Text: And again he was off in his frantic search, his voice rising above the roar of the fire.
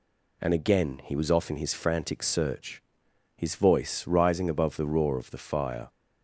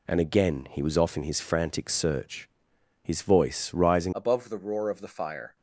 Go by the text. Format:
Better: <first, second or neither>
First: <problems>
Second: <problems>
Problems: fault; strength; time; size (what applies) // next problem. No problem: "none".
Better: first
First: none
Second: changes voice at "above"; from 4.1 s on; 1.4 s long